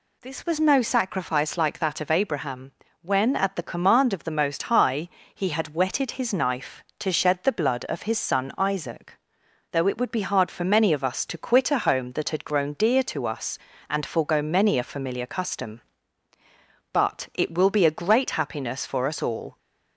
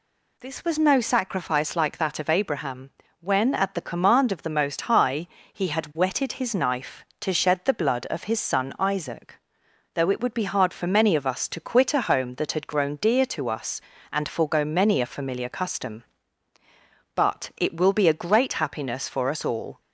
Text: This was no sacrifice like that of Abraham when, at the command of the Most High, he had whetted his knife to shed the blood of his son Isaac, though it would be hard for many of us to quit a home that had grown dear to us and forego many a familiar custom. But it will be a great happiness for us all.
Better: neither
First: pauses between "Abraham" and "when"; slight; at 2.7 s; 0.30 s long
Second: pauses between "Abraham" and "when"; slight; at 2.9 s; 0.30 s long

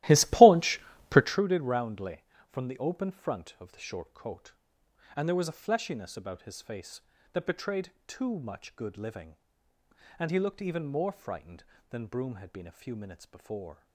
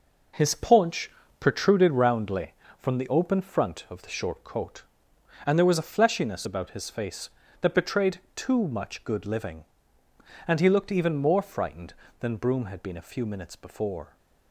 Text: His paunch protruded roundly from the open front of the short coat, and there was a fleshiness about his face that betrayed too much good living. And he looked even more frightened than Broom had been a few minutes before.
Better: second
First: starts louder than the rest; strong; until 1.4 s; 16 dB // pauses between "paunch" and "protruded"; slight; at 0.8 s; 0.26 s long // pauses between "betrayed" and "too"; slight; at 7.9 s; 0.16 s long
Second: pauses between "paunch" and "protruded"; slight; at 1.1 s; 0.26 s long // pauses between "betrayed" and "too"; slight; at 8.1 s; 0.16 s long

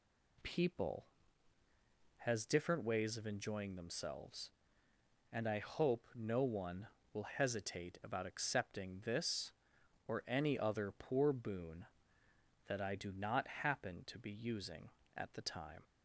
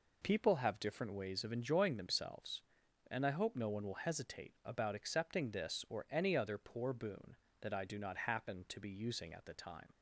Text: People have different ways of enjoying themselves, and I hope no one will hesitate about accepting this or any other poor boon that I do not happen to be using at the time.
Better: second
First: says "has" for "have"; at 2.1 s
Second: none

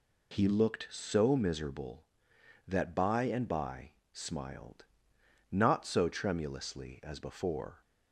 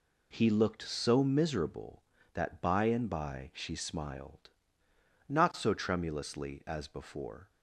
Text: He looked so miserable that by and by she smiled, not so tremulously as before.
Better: second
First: skips "she"; at 4.0 s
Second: none

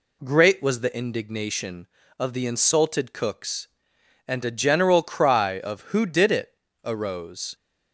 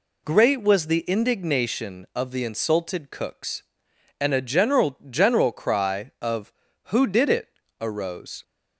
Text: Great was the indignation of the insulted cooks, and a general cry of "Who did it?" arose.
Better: first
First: none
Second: says "general" twice; at 5.1 s

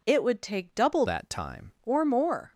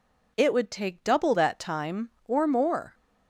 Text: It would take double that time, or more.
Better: second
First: changes voice from "that" to "time"; from 1.0 to 1.7 s; 0.7 s long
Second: none

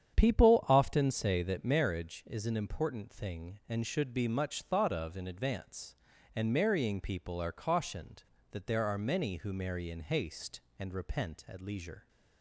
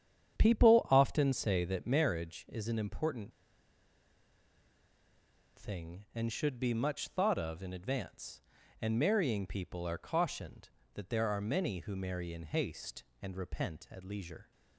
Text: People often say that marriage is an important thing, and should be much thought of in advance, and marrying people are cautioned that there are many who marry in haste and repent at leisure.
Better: first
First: starts louder than the rest; strong; until 1.1 s; 8.5 dB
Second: starts louder than the rest; strong; until 1.4 s; 8.5 dB // pauses between "important" and "thing"; strong; at 3.3 s; 2.2 s long

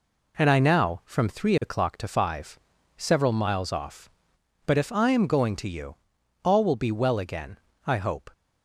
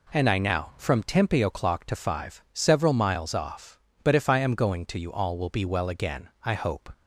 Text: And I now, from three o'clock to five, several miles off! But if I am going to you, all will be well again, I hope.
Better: first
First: none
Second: says "tempe" for "three"; at 1.0 s

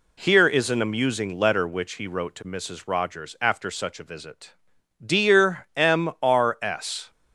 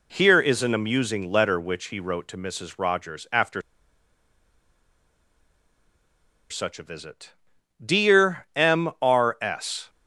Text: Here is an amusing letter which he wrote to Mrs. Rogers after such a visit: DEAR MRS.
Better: first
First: none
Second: pauses between "after" and "such"; strong; at 3.6 s; 2.8 s long

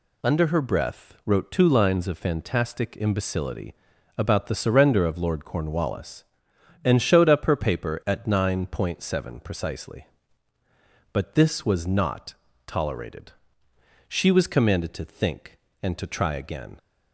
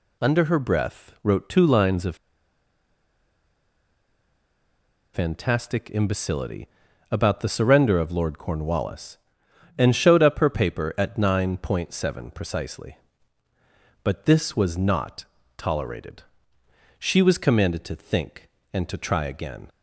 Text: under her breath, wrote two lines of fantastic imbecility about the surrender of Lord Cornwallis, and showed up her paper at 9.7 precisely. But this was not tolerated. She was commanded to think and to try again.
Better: first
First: pauses between "imbecility" and "about"; at 3.7 s; 0.42 s long // pauses between "not" and "tolerated"; slight; at 12.3 s; 0.32 s long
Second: pauses between "of" and "fantastic"; strong; at 2.1 s; 2.9 s long // pauses between "imbecility" and "about"; at 6.6 s; 0.42 s long // pauses between "not" and "tolerated"; slight; at 15.2 s; 0.32 s long

